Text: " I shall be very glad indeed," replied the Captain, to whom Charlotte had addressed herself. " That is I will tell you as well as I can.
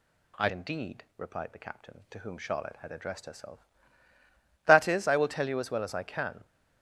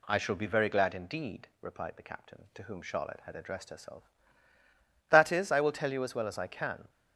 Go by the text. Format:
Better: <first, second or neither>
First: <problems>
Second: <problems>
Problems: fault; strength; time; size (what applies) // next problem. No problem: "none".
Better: second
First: skips "shall be very glad"; at 0.4 s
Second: none